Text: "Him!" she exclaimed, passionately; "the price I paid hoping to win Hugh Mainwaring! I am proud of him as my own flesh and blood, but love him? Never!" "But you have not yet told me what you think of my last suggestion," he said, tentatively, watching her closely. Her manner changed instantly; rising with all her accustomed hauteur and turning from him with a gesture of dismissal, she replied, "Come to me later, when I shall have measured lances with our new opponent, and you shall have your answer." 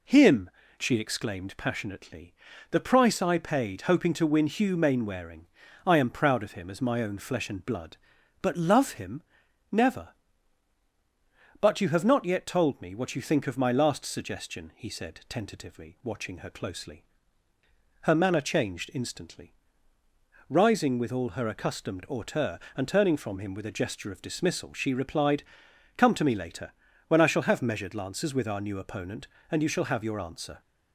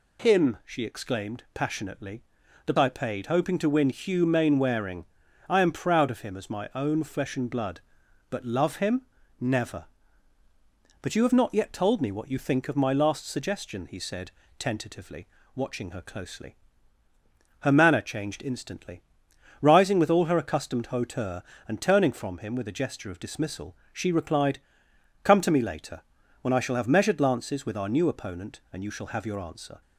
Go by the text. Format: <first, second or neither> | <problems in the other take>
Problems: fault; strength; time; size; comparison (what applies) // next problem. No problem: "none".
first | skips "price"; at 2.7 s